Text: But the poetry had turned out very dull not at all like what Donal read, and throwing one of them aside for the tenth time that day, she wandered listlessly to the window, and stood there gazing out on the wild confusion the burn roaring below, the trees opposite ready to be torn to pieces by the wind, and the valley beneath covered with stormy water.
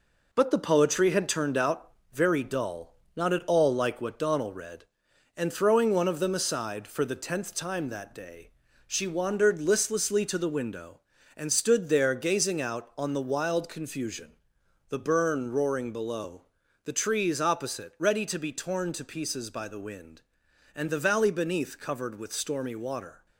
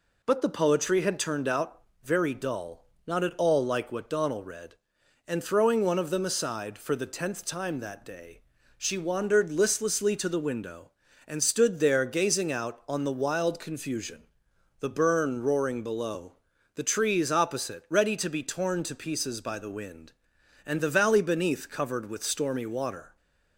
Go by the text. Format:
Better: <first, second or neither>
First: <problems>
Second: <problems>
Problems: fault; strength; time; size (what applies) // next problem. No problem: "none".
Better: second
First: gets quieter; noticeable; throughout; 5.5 dB // pauses between "out" and "very"; slight; at 1.9 s; 0.22 s long // pauses between "dull" and "not"; slight; at 2.8 s; 0.26 s long // pauses between "confusion" and "the"; noticeable; at 14.3 s; 0.56 s long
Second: pauses between "out" and "very"; slight; at 1.8 s; 0.22 s long // pauses between "dull" and "not"; slight; at 2.8 s; 0.26 s long // pauses between "confusion" and "the"; noticeable; at 14.2 s; 0.56 s long